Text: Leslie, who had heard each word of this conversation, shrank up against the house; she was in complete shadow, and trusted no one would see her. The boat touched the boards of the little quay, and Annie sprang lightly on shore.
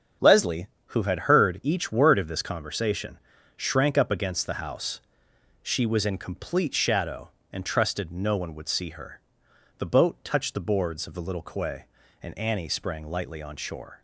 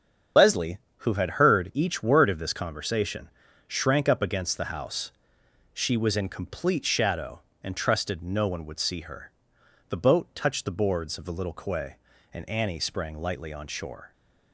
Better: first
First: starts louder than the rest; strong; until 1.4 s; 7.5 dB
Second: loses the start of "Leslie"; at 0.3 s; 40 ms // starts louder than the rest; strong; until 1.5 s; 8 dB

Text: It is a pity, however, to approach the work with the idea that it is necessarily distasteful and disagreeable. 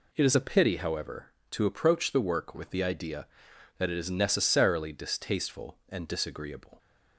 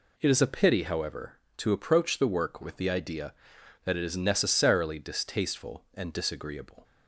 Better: neither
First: none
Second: none

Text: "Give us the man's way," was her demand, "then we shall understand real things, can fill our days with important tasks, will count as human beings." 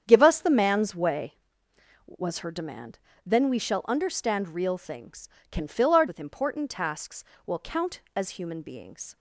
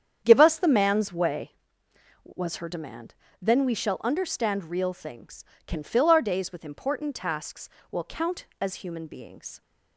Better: second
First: starts louder than the rest; strong; until 1.0 s; 8.5 dB // skips "days"; at 6.0 s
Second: starts louder than the rest; strong; until 1.2 s; 8.5 dB

